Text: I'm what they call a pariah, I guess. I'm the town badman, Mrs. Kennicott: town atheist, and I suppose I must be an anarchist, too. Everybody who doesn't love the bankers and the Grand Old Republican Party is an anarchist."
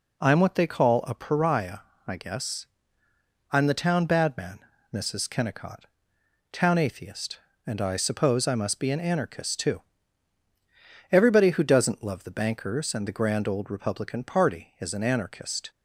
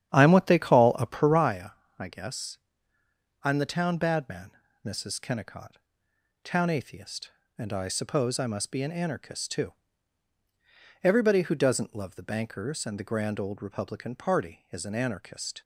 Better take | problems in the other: first | starts louder than the rest; strong; until 1.6 s; 9.5 dB

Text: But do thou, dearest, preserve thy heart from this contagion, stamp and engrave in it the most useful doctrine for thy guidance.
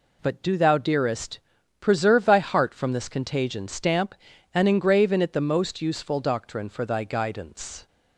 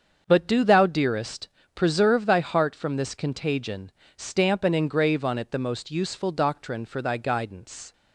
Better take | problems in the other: first | starts louder than the rest; until 1.2 s; 7 dB // says "on" for "in"; at 5.2 s

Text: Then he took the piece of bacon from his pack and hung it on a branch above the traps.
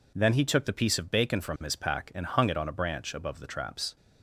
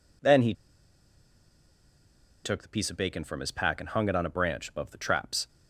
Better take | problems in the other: first | pauses between "he" and "took"; strong; at 0.5 s; 1.9 s long

